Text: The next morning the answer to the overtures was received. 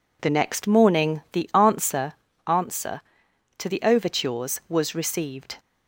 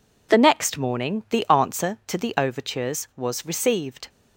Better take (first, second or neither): second